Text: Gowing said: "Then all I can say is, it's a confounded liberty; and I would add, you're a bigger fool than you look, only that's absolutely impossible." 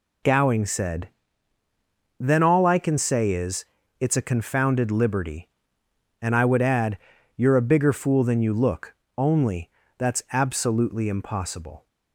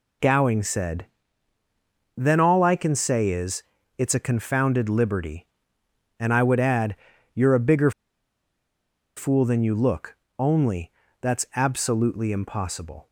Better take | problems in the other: first | pauses between "bigger" and "fool"; strong; at 7.9 s; 1.2 s long // pauses between "only" and "that's"; slight; at 10.9 s; 0.30 s long; slight in the first

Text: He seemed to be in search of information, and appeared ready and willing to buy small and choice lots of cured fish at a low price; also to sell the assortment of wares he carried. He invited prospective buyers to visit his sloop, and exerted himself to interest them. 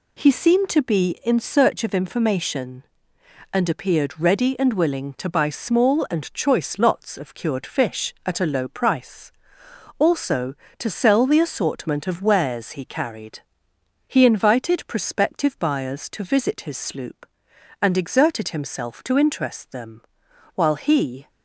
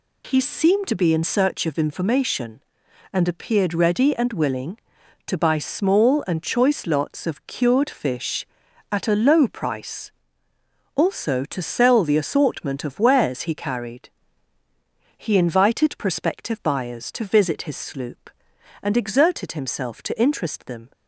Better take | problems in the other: second | goes on to say "While he"; noticeable; from 20.5 s on; 0.74 s long

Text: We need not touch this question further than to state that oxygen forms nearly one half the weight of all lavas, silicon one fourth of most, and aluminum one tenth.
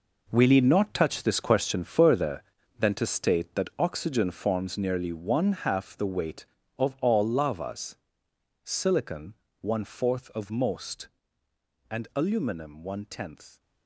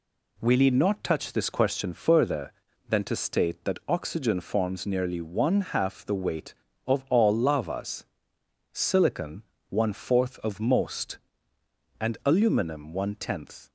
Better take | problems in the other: second | gets quieter; strong; throughout; 11.5 dB // pauses between "silicon" and "one"; slight; at 9.3 s; 0.26 s long; slight in the second

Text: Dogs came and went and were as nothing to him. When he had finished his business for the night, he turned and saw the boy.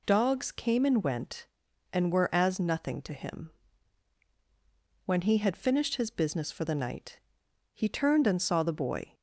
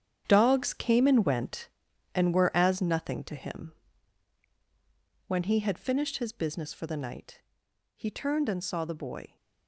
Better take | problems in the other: first | gets quieter; strong; throughout; 11.5 dB

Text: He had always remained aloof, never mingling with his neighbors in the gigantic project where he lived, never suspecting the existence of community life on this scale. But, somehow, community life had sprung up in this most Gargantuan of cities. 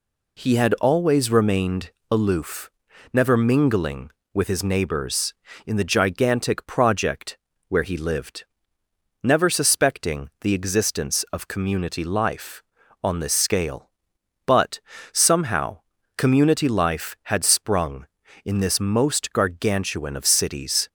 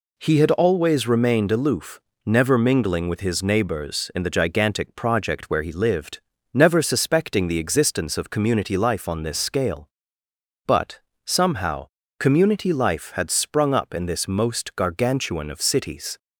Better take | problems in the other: second | pauses between "remained" and "aloof"; slight; at 1.8 s; 0.22 s long // pauses between "project" and "where"; slight; at 7.3 s; 0.32 s long // skips "up"; at 18.2 s

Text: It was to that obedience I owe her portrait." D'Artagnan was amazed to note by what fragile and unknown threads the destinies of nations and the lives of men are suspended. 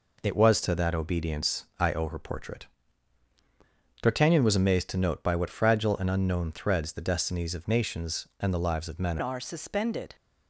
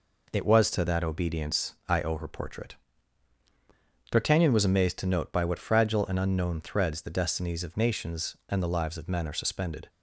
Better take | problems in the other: second | changes voice at "are"; from 9.1 s on; 1.0 s long

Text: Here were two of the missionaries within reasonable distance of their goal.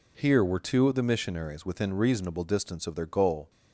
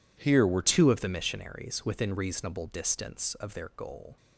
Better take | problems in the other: first | changes voice at "two"; from 0.6 s on; 3.5 s long

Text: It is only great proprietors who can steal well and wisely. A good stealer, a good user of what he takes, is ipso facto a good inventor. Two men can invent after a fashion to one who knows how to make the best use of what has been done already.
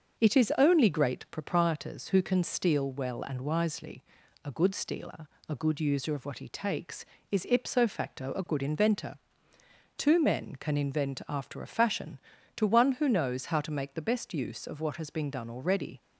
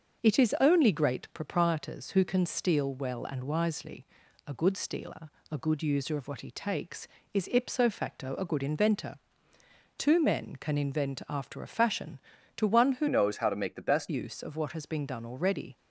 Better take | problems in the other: first | starts louder than the rest; until 1.2 s; 6.5 dB; also in the first // changes voice from "knows" to "best"; from 13.0 to 14.0 s; 1.0 s long

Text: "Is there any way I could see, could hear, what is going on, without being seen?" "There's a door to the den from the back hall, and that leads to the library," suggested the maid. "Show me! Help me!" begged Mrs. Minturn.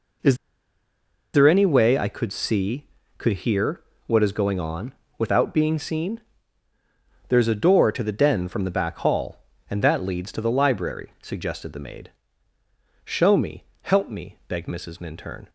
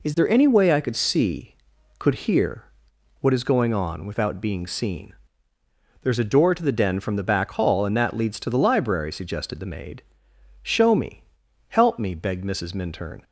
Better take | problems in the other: second | pauses between "Is" and "there"; at 0.3 s; 0.98 s long

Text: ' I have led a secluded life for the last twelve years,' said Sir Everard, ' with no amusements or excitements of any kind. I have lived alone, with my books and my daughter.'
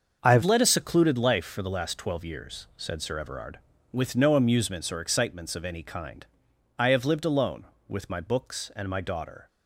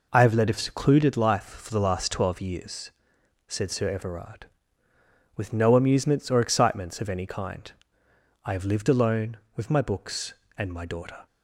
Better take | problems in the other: second | starts louder than the rest; until 1.2 s; 6.5 dB // changes voice at "led"; from 0.4 s on; 9.0 s long

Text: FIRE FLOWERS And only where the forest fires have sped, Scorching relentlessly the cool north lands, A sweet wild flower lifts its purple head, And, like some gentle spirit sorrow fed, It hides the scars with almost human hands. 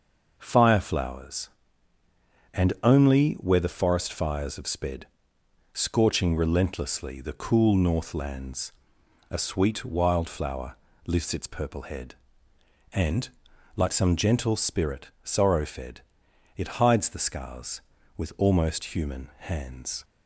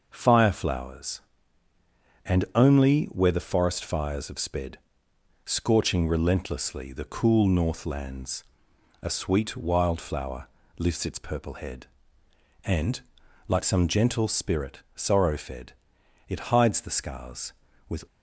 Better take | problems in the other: first | starts louder than the rest; noticeable; until 1.1 s; 6 dB; noticeable in the first // pauses between "flower" and "lifts"; slight; at 10.4 s; 0.30 s long; slight in the first // stops before "almost human hands"; at 18.0 s

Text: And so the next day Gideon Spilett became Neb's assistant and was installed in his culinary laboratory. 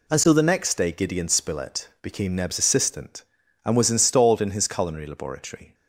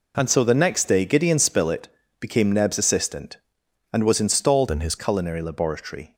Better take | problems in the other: first | pauses between "Spilett" and "became"; slight; at 1.8 s; 0.32 s long // changes voice from "in" to "his"; from 4.7 to 4.9 s; 0.2 s long

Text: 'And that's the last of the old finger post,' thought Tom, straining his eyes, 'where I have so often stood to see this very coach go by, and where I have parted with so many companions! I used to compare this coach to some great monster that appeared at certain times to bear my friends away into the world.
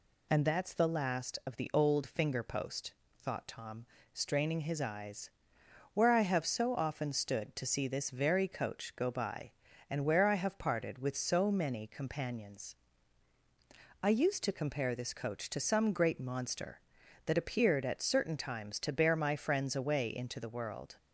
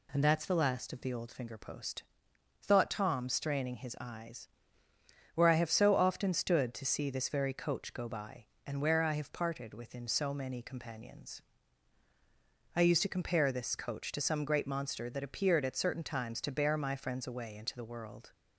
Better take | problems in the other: first | says "within" for "with"; at 9.7 s

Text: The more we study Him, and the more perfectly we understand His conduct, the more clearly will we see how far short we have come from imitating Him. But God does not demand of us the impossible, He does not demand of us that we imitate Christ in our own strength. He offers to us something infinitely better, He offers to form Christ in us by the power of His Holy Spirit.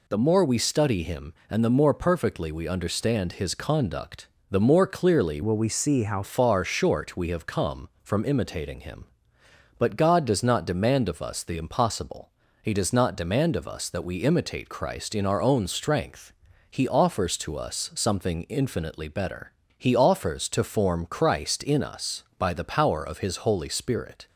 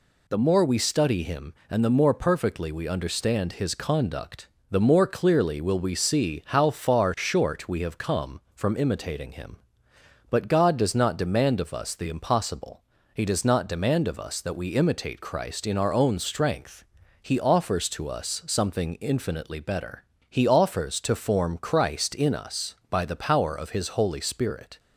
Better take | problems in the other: second | changes voice from "will" to "how"; from 5.4 to 6.2 s; 0.8 s long

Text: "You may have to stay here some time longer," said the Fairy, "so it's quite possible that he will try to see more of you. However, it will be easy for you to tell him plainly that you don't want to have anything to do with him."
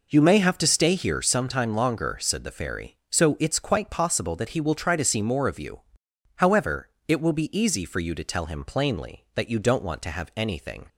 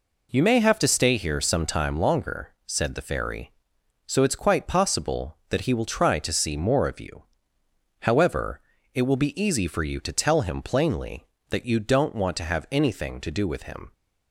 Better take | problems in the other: second | stops before "to do with him"; at 10.8 s

